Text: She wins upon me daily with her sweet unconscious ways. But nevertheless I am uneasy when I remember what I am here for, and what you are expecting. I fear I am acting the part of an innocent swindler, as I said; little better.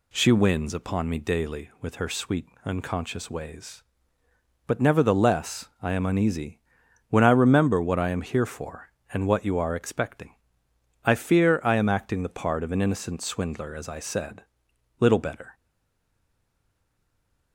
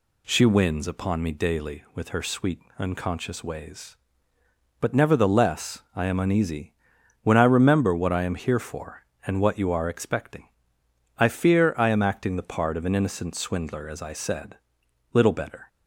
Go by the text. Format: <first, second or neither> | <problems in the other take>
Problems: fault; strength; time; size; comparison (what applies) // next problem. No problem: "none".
second | pauses between "sweet" and "unconscious"; slight; at 2.4 s; 0.20 s long; slight in the second // pauses between "uneasy" and "when"; noticeable; at 6.6 s; 0.48 s long; noticeable in the second // stays silent after the last word; noticeable; from 15.5 s on; 2.0 s long